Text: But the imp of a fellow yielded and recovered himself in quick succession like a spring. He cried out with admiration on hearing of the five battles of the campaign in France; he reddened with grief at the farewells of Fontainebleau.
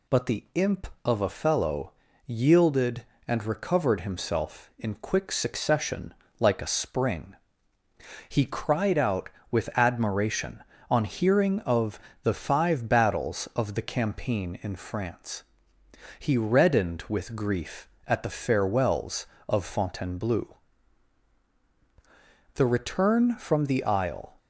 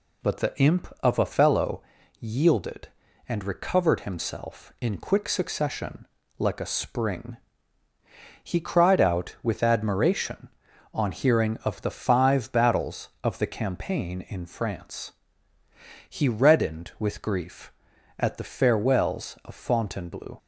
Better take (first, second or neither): second